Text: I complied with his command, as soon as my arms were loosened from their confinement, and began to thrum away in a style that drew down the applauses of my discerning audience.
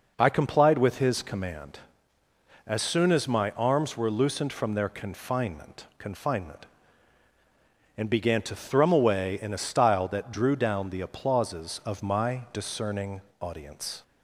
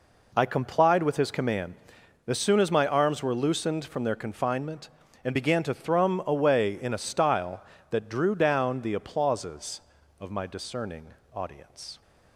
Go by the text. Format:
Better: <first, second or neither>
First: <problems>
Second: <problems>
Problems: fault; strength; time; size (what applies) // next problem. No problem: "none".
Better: second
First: says "confinement" twice; at 5.9 s // pauses between "discerning" and "audience"; slight; at 13.2 s; 0.18 s long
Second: pauses between "discerning" and "audience"; slight; at 11.0 s; 0.28 s long